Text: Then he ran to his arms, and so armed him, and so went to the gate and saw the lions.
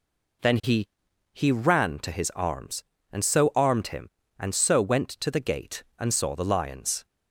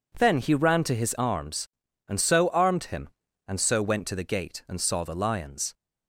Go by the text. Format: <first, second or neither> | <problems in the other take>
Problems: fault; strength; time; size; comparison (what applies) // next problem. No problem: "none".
second | says "he" twice; at 1.3 s